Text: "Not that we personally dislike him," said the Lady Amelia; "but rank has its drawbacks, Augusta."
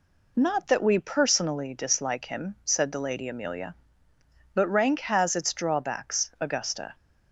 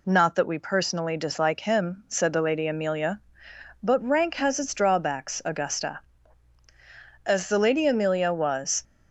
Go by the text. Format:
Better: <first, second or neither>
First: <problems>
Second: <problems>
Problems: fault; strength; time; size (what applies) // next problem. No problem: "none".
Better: first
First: none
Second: goes on to say "As the Lady Amelia was"; from 7.2 s on; 1.5 s long